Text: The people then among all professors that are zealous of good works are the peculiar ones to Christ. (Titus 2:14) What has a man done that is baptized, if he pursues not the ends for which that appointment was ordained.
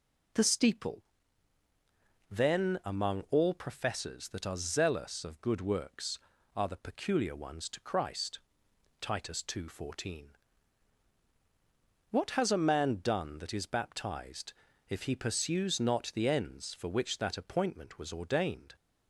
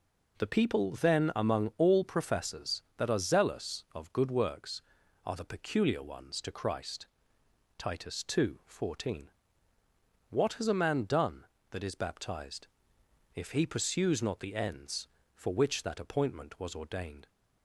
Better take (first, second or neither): second